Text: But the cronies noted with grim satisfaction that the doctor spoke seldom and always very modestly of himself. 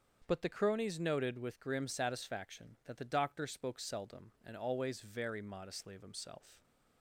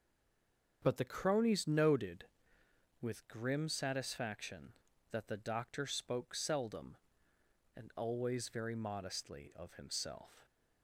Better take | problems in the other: first | stays silent before the first word; slight; until 0.8 s; 0.8 s long // starts louder than the rest; until 1.8 s; 7 dB; also in the first

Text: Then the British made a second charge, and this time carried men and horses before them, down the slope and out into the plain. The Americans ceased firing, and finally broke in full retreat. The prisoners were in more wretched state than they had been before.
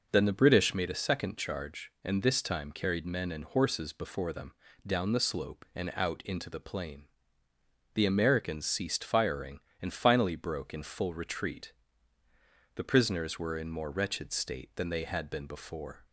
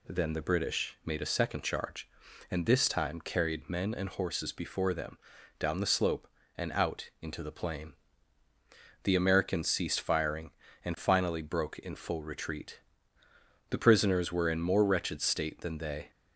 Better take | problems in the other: first | stops before "had been before"; at 16.1 s

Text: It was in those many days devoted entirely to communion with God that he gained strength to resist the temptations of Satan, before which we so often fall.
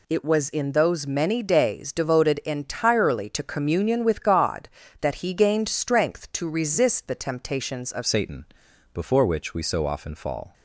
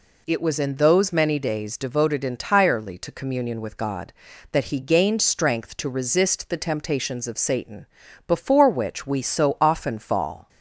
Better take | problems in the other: second | changes voice at "Satan"; from 8.0 s on; 2.5 s long

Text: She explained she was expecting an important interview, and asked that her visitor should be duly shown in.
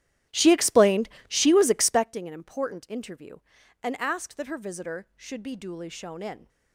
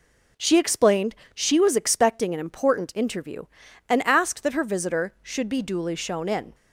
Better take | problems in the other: second | starts louder than the rest; strong; until 2.1 s; 13 dB // pauses between "explained" and "she"; slight; at 1.0 s; 0.18 s long; slight in the second

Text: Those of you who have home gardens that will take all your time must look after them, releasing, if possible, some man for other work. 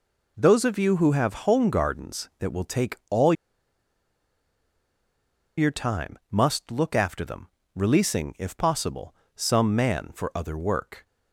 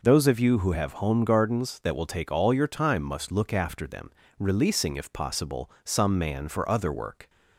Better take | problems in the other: second | pauses between "all" and "your"; strong; at 3.3 s; 2.2 s long

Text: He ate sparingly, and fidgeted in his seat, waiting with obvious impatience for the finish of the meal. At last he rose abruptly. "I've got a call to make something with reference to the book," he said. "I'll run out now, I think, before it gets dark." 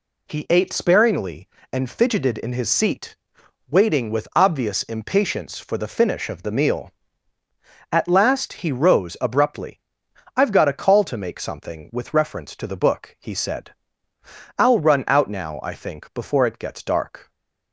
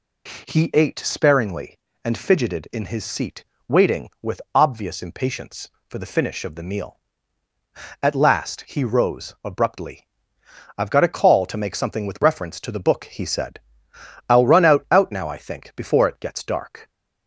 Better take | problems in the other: first | says "out" twice; at 14.8 s

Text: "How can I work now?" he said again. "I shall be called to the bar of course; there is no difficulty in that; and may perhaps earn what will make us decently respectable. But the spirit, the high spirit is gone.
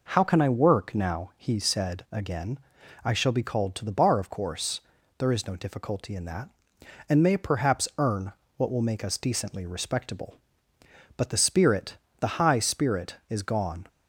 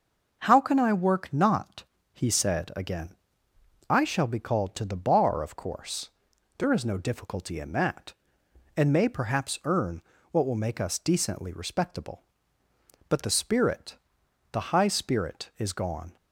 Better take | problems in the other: first | starts louder than the rest; until 1.4 s; 6.5 dB // says "not" for "now"; at 1.3 s // pauses between "earn" and "what"; slight; at 9.9 s; 0.32 s long; slight in the first

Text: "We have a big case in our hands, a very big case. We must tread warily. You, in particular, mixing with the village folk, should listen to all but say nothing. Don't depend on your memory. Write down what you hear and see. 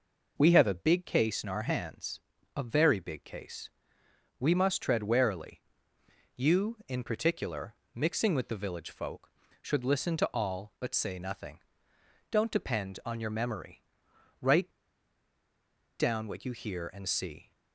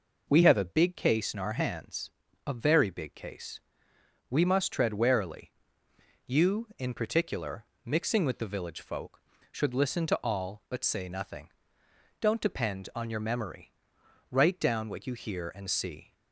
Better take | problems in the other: second | pauses between "Write" and "down"; strong; at 14.6 s; 1.3 s long

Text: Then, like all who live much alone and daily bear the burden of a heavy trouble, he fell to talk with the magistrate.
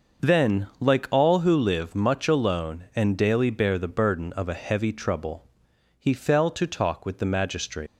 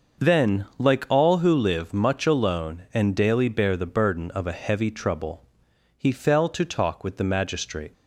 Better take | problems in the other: second | starts louder than the rest; noticeable; until 1.3 s; 6 dB; also in the second // leaves "magistrate" unfinished; at 7.8 s; 80 ms

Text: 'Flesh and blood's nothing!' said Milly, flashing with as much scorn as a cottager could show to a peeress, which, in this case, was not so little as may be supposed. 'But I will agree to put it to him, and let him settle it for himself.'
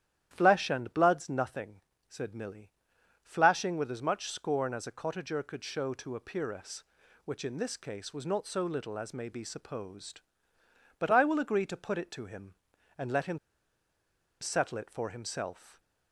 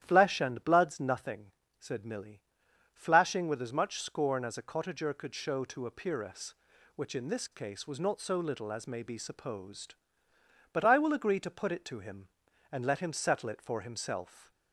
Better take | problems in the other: second | starts louder than the rest; strong; until 1.3 s; 11 dB; strong in the second // pauses between "him" and "settle"; at 13.3 s; 1.0 s long

